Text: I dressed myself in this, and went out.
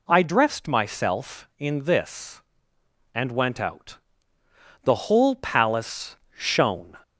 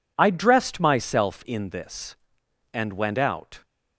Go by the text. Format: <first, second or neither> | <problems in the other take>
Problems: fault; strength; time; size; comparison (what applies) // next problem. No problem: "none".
second | goes on to say "The whole palace shone"; strong; from 4.8 s on; 2.1 s long